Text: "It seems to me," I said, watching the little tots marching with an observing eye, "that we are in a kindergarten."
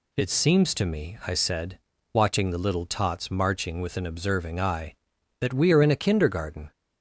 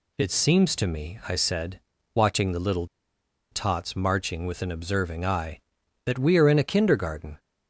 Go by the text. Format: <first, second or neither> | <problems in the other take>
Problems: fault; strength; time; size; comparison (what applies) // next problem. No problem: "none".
first | pauses between "little" and "tots"; noticeable; at 2.8 s; 0.66 s long